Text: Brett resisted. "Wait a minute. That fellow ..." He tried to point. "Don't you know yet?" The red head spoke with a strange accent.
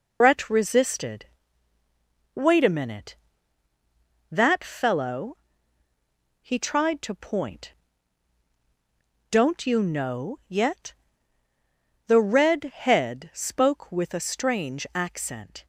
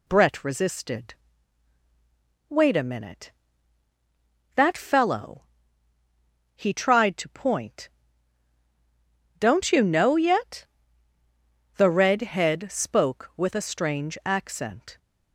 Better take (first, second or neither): second